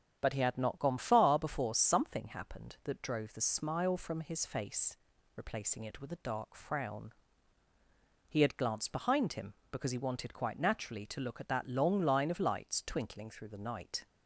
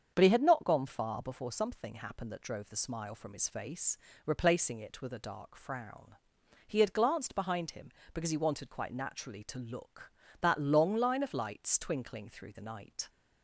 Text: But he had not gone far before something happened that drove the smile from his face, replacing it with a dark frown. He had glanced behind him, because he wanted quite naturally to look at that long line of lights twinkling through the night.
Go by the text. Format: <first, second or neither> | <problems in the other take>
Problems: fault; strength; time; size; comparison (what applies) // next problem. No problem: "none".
first | starts louder than the rest; strong; until 1.1 s; 7 dB; strong in the first // skips "at"; at 10.2 s